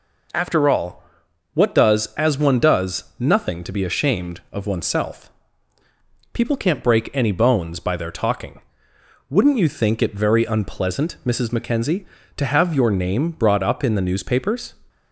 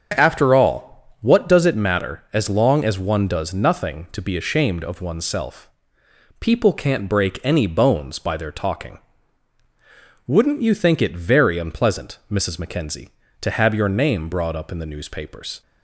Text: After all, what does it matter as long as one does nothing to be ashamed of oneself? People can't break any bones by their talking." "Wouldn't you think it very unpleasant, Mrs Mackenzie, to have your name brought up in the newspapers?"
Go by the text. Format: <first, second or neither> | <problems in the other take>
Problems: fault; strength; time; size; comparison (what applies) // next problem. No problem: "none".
second | skips "it matter as long"; at 2.1 s